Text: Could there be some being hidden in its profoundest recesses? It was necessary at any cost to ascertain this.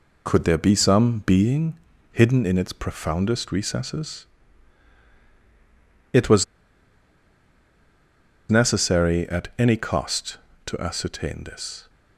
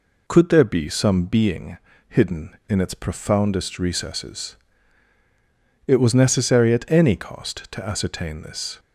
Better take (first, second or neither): second